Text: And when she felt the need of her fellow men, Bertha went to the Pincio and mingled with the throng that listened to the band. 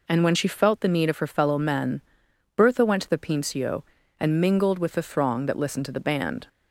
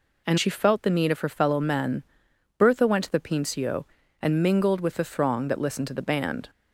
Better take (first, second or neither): first